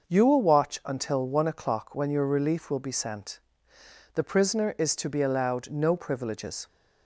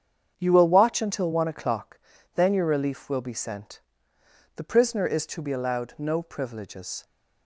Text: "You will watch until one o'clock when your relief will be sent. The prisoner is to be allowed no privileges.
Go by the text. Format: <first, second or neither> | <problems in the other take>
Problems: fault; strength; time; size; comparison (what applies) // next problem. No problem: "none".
first | starts louder than the rest; strong; until 1.3 s; 7.5 dB; noticeable in the first // says "then" for "when"; at 2.3 s